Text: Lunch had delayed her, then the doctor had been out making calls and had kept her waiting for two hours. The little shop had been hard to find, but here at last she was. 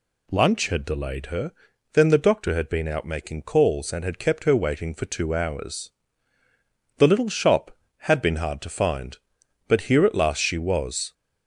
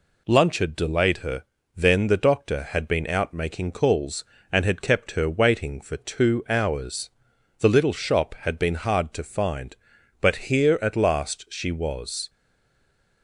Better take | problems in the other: first | stays silent after the last word; slight; from 12.2 s on; 1.0 s long

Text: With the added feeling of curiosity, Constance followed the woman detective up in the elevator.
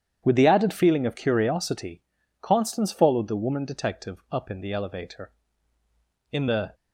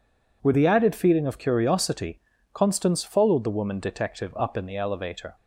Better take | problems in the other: second | starts louder than the rest; strong; until 1.2 s; 9 dB // goes on to say "In the"; slight; from 6.3 s on; 0.43 s long

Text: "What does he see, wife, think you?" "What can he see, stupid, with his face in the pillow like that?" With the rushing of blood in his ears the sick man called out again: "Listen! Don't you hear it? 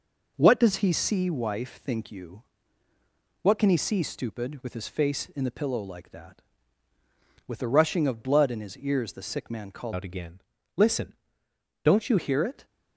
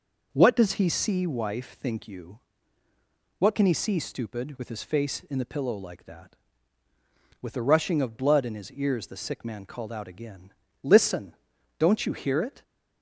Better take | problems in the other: second | changes voice from "out" to "you"; from 9.9 to 12.1 s; 2.2 s long

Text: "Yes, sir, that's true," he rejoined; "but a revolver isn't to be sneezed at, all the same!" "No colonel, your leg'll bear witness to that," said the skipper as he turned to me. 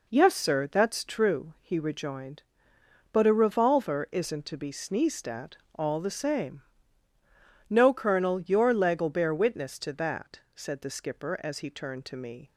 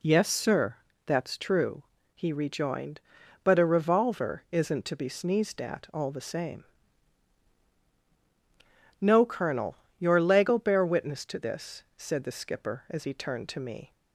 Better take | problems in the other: first | says "this" for "that"; at 11.3 s

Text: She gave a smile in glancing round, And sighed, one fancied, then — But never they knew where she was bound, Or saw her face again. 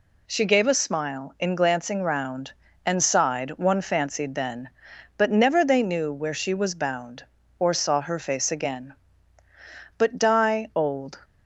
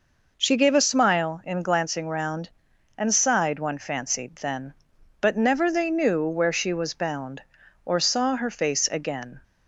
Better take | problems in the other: second | goes on to say "But die old"; noticeable; from 9.9 s on; 1.2 s long

